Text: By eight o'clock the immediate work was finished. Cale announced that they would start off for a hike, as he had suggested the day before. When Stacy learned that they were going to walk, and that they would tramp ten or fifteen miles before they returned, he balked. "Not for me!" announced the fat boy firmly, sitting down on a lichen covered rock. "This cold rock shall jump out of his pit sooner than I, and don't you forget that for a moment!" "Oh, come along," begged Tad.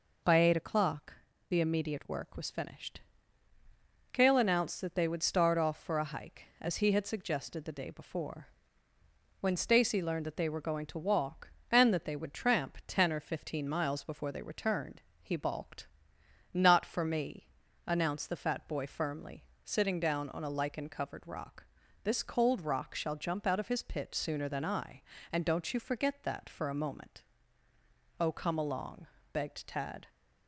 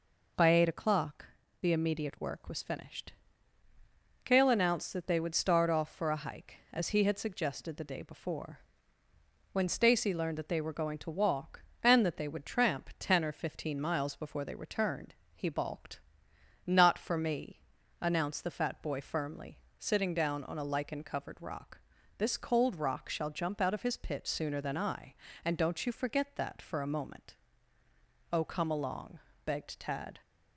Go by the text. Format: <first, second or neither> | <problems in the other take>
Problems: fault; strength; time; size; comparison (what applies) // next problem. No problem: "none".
neither | pauses between "o'clock" and "the"; slight; the same in both